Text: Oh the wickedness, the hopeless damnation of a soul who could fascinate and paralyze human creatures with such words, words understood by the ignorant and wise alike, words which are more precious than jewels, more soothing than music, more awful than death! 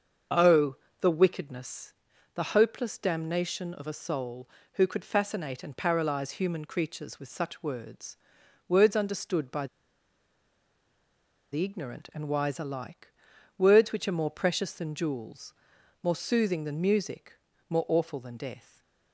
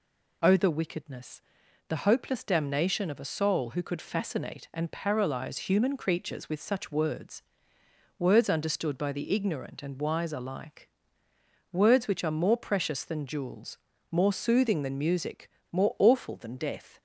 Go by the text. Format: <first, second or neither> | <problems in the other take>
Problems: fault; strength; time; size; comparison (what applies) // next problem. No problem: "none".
second | starts louder than the rest; until 1.6 s; 6.5 dB // pauses between "Oh" and "the"; slight; at 0.7 s; 0.26 s long // pauses between "by" and "the"; strong; at 9.6 s; 1.8 s long // stays silent after the last word; slight; from 18.6 s on; 0.5 s long